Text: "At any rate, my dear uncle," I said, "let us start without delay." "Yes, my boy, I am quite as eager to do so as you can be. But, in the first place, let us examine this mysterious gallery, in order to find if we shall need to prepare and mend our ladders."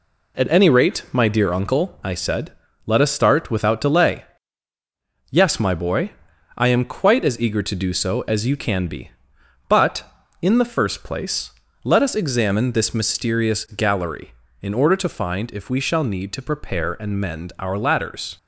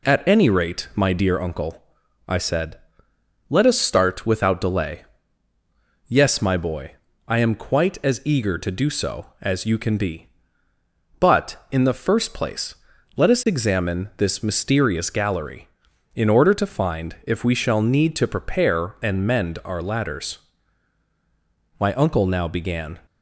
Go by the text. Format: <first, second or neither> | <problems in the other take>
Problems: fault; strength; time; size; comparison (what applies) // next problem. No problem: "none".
first | goes on to say "My uncle now began"; noticeable; from 21.7 s on; 1.2 s long